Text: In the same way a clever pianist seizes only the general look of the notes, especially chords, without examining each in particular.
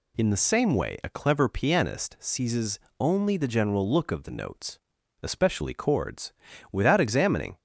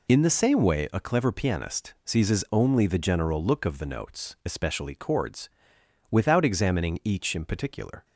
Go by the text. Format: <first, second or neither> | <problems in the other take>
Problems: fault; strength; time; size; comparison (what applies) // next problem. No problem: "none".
second | pauses between "seizes" and "only"; slight; at 2.7 s; 0.20 s long // stops before "each in particular"; at 7.5 s